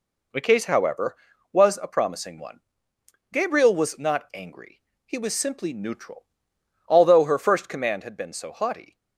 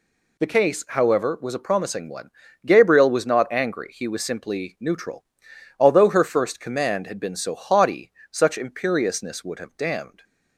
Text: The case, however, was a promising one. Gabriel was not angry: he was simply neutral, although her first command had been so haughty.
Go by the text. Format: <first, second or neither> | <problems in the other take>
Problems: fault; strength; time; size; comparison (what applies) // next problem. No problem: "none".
first | goes on to say "Such imperiousness would have damned"; strong; from 8.3 s on; 1.9 s long